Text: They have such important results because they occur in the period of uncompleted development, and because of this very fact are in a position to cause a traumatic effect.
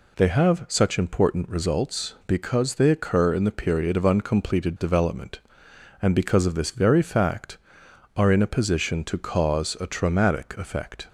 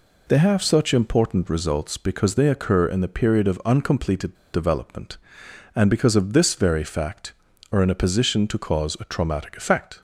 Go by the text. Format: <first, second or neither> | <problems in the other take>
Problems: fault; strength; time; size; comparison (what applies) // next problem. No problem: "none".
first | pauses between "uncompleted" and "development"; slight; at 4.3 s; 0.17 s long